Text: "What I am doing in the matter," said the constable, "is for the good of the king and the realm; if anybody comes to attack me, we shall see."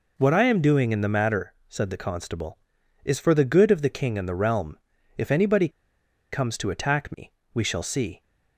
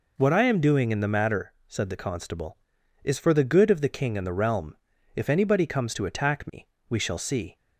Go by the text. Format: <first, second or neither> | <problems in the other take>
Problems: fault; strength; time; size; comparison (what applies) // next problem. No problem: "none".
second | pauses between "anybody" and "comes"; noticeable; at 5.6 s; 0.63 s long